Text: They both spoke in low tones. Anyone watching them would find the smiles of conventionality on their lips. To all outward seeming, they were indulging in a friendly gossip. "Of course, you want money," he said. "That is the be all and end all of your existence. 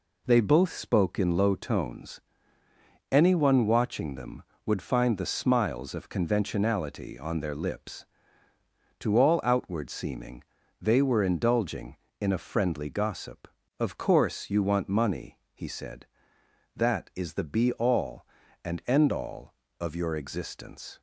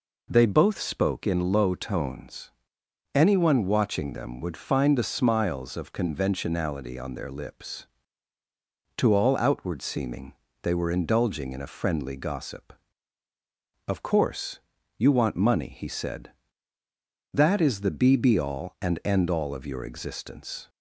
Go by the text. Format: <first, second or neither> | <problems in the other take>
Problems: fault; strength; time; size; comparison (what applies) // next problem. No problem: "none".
first | says "be" twice; at 18.1 s